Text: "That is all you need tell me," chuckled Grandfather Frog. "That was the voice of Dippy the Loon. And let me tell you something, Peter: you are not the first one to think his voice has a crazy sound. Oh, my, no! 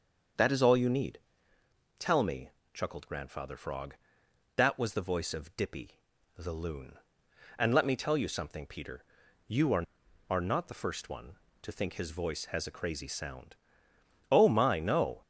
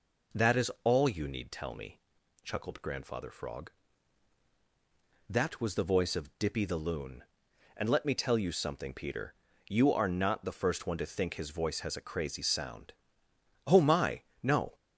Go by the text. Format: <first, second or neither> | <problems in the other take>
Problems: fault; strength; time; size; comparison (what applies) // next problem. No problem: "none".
second | starts louder than the rest; until 2.1 s; 6.5 dB // pauses between "need" and "tell"; noticeable; at 1.2 s; 0.76 s long // pauses between "Dippy" and "the"; at 5.9 s; 0.38 s long // says "are" twice; at 10.2 s